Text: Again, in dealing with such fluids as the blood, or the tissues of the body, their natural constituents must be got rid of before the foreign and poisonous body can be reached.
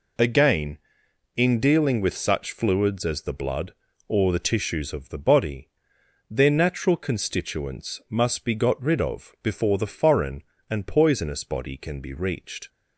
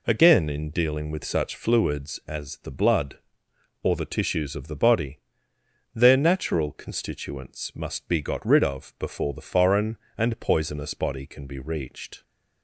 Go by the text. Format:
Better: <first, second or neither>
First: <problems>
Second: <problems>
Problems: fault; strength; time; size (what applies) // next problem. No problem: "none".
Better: neither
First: none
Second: none